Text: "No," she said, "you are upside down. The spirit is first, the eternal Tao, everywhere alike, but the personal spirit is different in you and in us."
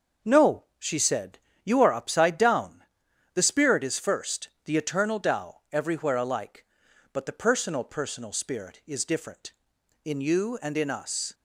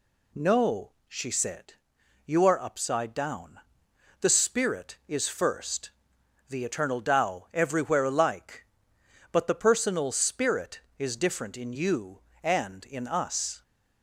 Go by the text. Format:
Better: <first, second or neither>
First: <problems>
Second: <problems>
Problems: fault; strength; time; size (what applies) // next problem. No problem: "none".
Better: second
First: starts louder than the rest; until 1.3 s; 6 dB // says "personal" twice; at 7.8 s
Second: none